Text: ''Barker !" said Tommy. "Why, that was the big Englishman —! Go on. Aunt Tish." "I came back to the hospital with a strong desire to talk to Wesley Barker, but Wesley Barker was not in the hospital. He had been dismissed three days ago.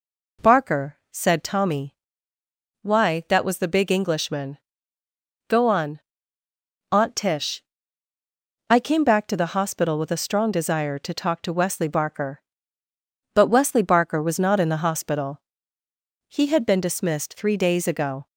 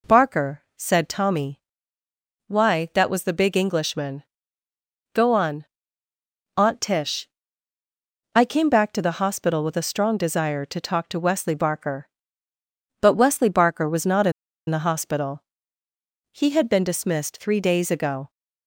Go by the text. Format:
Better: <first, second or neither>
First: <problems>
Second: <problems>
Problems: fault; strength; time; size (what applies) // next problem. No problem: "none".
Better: first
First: none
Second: pauses between "in" and "the"; at 14.3 s; 0.38 s long